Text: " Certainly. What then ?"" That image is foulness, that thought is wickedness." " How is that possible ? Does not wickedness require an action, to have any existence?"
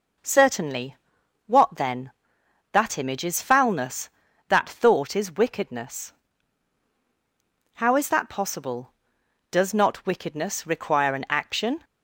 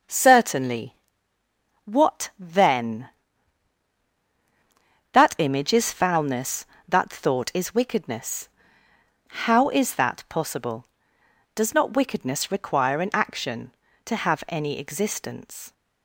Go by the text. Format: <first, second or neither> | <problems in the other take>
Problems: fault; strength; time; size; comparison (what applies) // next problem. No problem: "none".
second | stops before "to have any existence"; at 11.8 s